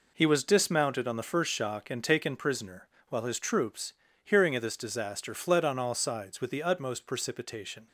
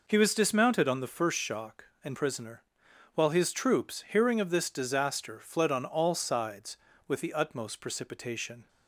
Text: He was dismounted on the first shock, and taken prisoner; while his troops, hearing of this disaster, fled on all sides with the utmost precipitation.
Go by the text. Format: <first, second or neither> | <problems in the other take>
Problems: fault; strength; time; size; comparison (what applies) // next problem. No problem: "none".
first | skips "taken"; at 2.1 s